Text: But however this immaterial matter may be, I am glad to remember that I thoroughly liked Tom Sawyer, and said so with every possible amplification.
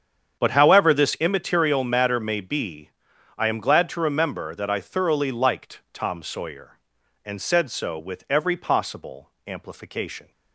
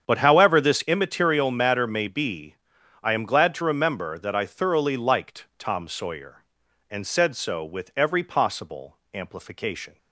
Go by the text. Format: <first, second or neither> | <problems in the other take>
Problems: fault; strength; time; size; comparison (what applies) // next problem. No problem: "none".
neither | starts louder than the rest; strong; the same in both // pauses between "possible" and "amplification"; slight; the same in both